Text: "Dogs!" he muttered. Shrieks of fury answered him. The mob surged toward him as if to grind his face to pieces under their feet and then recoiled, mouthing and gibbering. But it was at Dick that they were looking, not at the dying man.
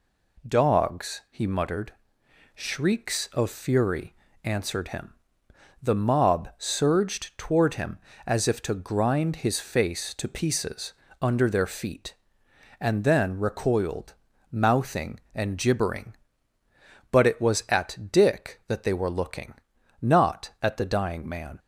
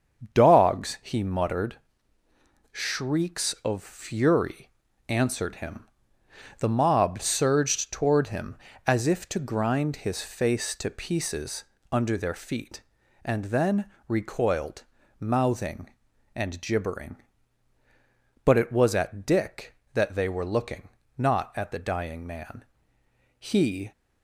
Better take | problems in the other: first | starts louder than the rest; until 1.4 s; 7 dB // pauses between "fury" and "answered"; slight; at 4.7 s; 0.36 s long; slight in the first // pauses between "pieces" and "under"; slight; at 11.6 s; 0.26 s long; slight in the first // pauses between "then" and "recoiled"; slight; at 13.8 s; 0.18 s long // goes on to say "He"; from 23.3 s on; 0.54 s long

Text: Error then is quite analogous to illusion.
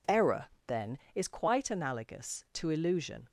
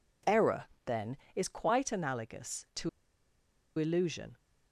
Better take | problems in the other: first | pauses between "Error" and "then"; slight; at 0.6 s; 0.18 s long; slight in the first // pauses between "to" and "illusion"; noticeable; at 2.8 s; 0.89 s long

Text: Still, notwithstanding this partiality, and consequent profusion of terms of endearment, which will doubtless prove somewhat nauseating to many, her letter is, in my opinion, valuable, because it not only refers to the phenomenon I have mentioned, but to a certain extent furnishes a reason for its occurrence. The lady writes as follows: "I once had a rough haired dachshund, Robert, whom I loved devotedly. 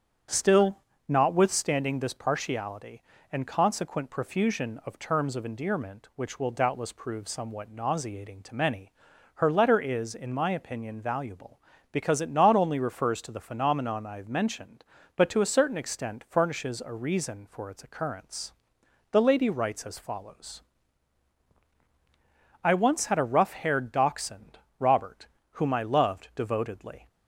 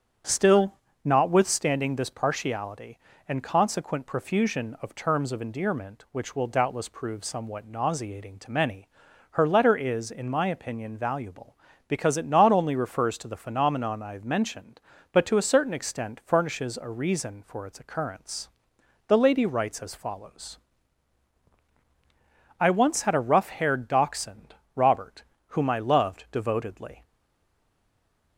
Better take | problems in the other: first | starts louder than the rest; strong; until 1.5 s; 8 dB; strong in the first // stays silent after the last word; noticeable; from 27.0 s on; 1.3 s long

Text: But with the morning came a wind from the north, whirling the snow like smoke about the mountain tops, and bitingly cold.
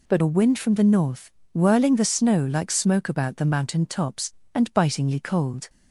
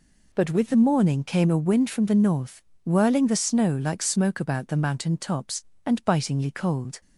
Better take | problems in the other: second | skips "with the morning came"; at 0.2 s

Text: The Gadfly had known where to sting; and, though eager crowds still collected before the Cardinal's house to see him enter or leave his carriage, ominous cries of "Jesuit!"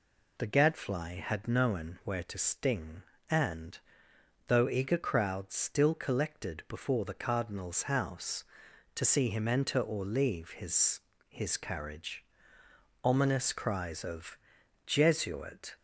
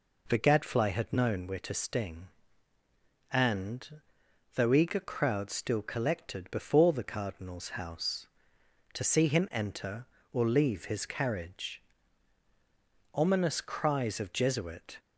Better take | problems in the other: second | says "his" twice; at 11.2 s // pauses between "of" and "Jesuit"; noticeable; at 14.3 s; 0.48 s long

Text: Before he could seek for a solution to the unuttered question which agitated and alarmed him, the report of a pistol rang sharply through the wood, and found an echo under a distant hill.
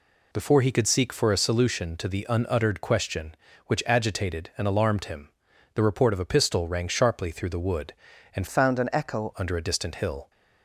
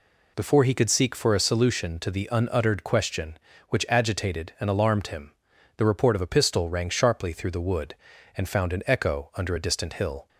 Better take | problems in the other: second | changes voice from "found" to "echo"; from 8.4 to 9.3 s; 0.9 s long

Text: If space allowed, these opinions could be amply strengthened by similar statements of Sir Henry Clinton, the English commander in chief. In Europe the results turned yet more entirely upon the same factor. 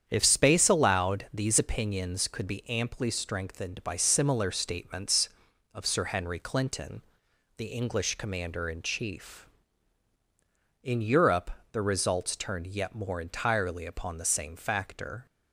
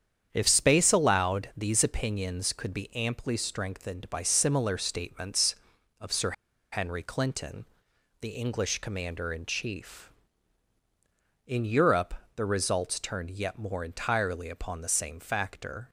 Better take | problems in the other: first | starts louder than the rest; strong; until 1.3 s; 8.5 dB; strong in the first // pauses between "Sir" and "Henry"; at 6.3 s; 0.40 s long // pauses between "Europe" and "the"; slight; at 12.1 s; 0.20 s long; slight in the first

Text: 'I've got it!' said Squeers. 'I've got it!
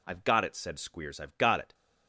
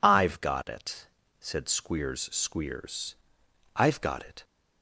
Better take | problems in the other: first | says "Squeers" twice; at 2.2 s

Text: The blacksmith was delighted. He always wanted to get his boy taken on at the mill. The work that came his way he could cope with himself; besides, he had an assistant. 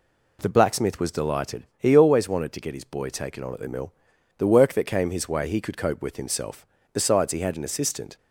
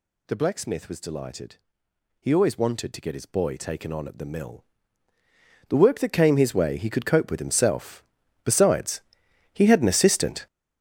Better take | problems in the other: first | gets louder; strong; throughout; 11 dB

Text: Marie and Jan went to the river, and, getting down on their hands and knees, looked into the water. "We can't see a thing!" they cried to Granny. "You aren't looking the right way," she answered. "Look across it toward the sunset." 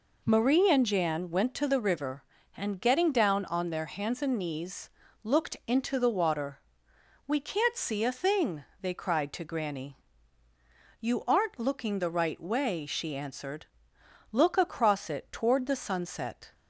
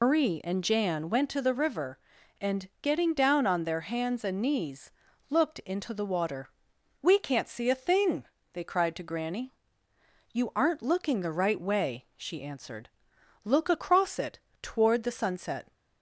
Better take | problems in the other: first | loses the start of "Marie"; at 0.0 s; 100 ms // pauses between "it" and "toward"; slight; at 14.3 s; 0.20 s long

